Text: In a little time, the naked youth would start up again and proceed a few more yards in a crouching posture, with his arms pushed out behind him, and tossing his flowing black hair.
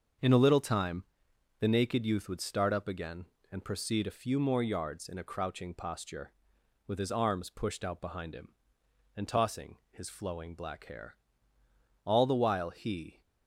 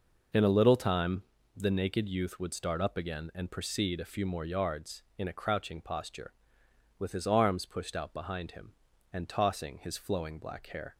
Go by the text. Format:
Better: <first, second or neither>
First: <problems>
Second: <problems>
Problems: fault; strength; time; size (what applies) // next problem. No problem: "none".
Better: second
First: starts louder than the rest; until 1.7 s; 6.5 dB // pauses between "tossing" and "his"; slight; at 9.7 s; 0.16 s long // goes on to say "All the while he"; noticeable; from 12.0 s on; 1.1 s long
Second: none